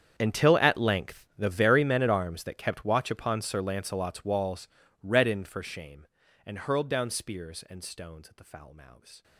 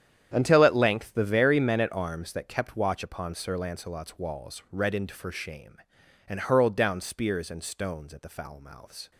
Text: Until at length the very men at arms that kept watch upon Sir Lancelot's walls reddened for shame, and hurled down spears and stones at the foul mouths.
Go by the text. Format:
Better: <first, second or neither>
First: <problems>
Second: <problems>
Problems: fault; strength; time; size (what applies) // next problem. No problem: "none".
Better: second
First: gets quieter; strong; throughout; 20 dB // starts louder than the rest; strong; until 1.1 s; 8 dB // pauses between "walls" and "reddened"; slight; at 4.6 s; 0.36 s long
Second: starts louder than the rest; strong; until 1.3 s; 9 dB